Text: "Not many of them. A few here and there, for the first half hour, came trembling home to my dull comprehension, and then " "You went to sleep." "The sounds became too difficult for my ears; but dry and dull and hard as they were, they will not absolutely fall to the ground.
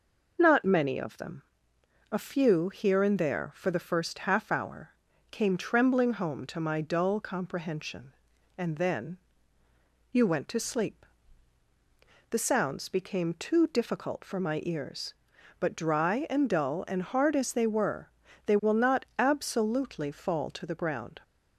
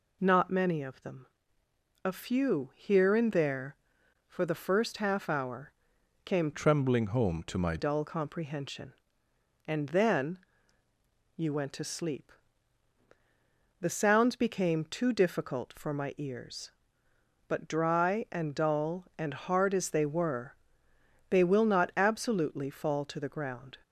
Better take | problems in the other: first | changes voice from "trembling" to "my"; from 6.5 to 7.7 s; 1.2 s long

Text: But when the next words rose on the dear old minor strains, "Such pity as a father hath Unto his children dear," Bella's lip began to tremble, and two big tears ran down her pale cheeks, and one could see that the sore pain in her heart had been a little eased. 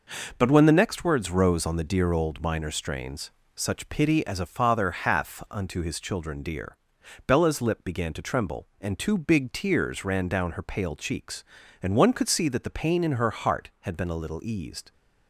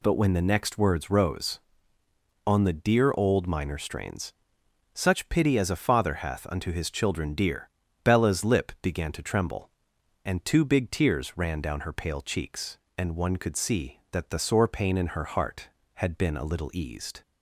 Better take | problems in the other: second | skips "sore"; at 12.7 s

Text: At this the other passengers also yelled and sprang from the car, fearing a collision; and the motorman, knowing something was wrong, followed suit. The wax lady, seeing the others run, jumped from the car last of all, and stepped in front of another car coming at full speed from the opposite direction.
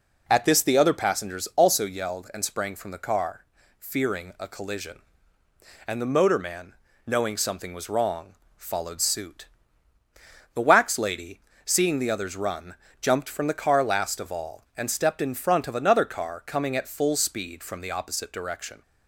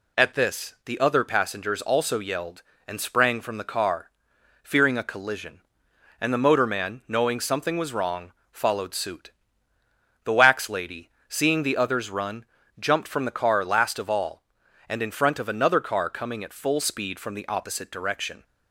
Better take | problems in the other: first | skips "stepped"; at 15.0 s

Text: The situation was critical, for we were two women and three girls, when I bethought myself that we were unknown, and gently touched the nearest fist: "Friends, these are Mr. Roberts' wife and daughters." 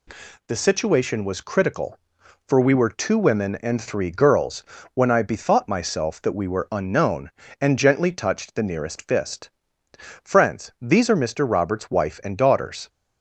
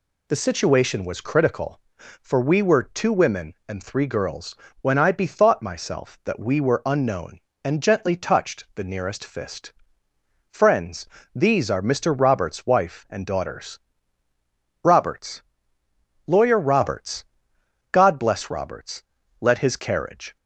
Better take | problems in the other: first | goes on to say "Roberts Lawyer Roberts God bless Roberts Let his carriage"; strong; from 14.8 s on; 5.5 s long

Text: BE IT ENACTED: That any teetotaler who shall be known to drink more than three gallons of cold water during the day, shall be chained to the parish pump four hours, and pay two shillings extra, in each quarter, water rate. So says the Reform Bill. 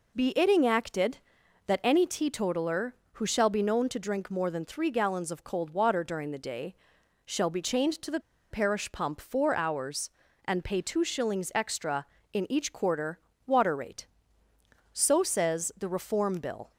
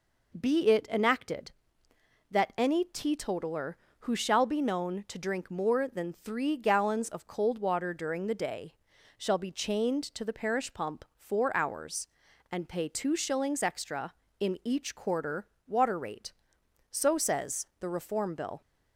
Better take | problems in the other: second | pauses between "the" and "parish"; slight; at 8.1 s; 0.31 s long

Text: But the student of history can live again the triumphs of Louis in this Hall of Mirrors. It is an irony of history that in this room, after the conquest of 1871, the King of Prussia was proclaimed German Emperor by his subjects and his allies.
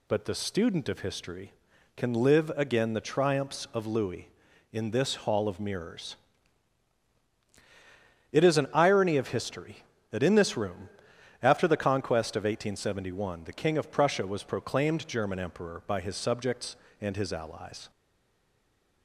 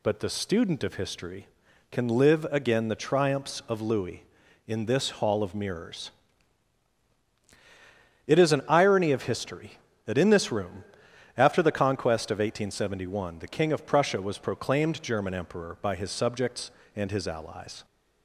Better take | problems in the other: second | stays silent after the last word; from 17.8 s on; 1.2 s long

